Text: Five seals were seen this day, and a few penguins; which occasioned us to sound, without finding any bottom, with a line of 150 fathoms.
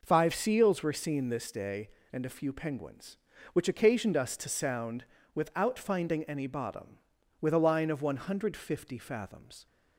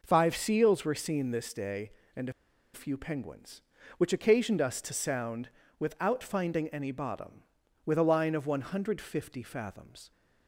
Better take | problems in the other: first | pauses between "a" and "few"; at 2.3 s; 0.42 s long

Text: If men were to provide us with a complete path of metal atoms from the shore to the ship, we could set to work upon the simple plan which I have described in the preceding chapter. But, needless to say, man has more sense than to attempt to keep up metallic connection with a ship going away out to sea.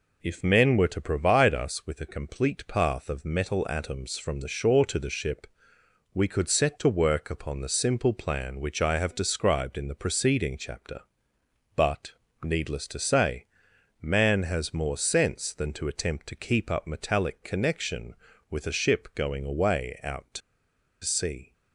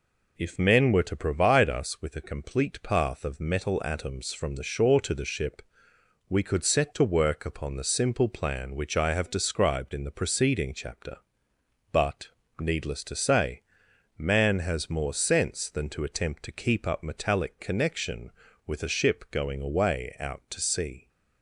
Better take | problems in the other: second | pauses between "to" and "sea"; noticeable; at 20.4 s; 0.64 s long

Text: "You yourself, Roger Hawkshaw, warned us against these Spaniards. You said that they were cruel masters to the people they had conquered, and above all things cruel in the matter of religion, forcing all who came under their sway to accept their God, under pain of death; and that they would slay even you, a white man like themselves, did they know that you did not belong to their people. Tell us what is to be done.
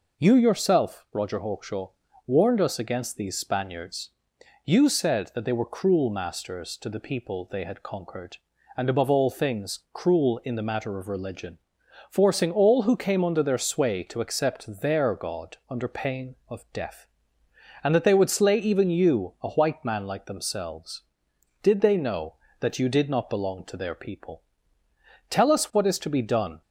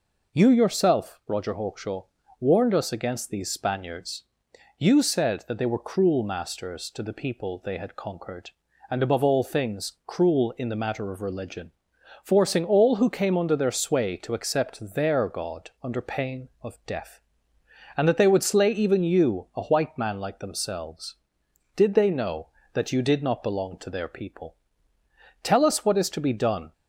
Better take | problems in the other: neither | none

